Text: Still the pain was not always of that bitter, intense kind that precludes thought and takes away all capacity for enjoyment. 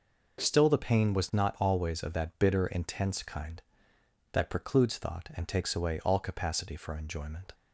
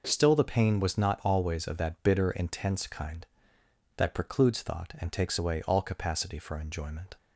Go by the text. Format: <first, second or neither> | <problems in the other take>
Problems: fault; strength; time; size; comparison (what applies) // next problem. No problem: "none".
neither | none